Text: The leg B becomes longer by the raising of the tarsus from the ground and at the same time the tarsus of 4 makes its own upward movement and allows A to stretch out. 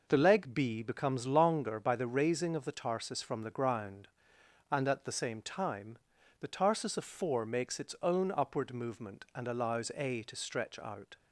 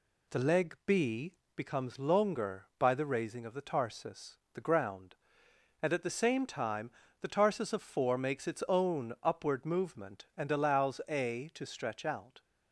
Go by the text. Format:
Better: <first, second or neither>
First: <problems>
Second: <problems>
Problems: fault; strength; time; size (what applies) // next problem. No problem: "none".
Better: first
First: pauses between "time" and "the"; at 5.9 s; 0.42 s long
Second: pauses between "B" and "becomes"; slight; at 1.3 s; 0.24 s long // skips "from"; at 4.4 s // pauses between "time" and "the"; slight; at 6.8 s; 0.32 s long